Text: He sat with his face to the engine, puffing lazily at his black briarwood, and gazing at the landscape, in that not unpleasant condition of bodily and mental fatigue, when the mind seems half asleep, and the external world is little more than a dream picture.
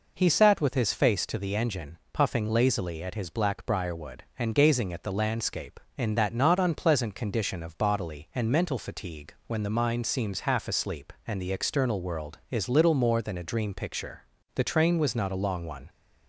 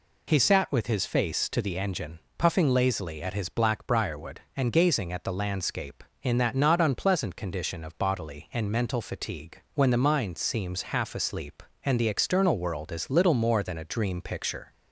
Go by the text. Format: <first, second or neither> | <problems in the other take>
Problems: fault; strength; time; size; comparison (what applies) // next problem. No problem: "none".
second | goes on to say "The train was not a long one"; from 14.5 s on; 1.3 s long